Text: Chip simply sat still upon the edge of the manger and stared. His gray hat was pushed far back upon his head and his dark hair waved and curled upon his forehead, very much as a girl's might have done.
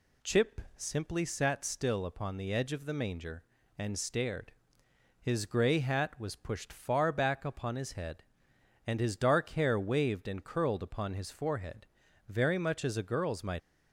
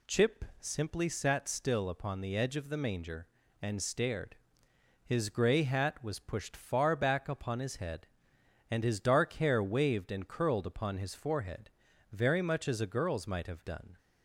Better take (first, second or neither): second